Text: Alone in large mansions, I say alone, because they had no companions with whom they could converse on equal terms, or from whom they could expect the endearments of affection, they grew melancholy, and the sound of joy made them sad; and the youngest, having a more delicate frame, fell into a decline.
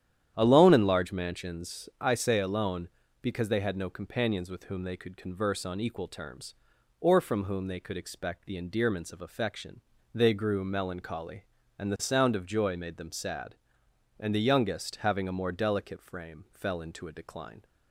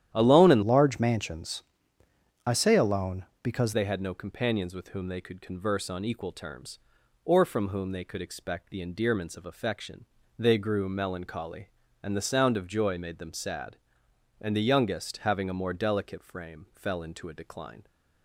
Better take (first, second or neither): first